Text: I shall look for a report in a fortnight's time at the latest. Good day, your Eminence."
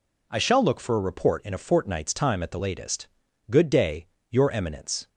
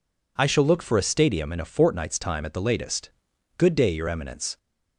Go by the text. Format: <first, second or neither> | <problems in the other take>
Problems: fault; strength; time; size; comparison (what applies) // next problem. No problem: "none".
first | says "stadium" for "report"; at 1.0 s